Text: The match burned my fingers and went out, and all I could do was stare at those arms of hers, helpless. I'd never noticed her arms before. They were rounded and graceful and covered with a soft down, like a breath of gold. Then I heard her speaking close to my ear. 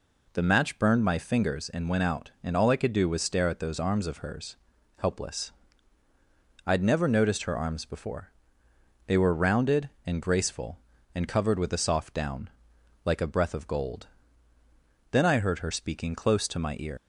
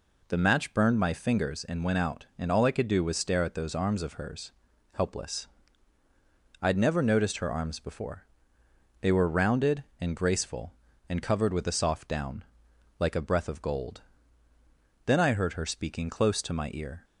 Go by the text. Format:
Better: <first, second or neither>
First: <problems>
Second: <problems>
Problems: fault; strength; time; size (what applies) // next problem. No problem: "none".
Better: second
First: leaves "ear" unfinished; at 16.9 s; 120 ms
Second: none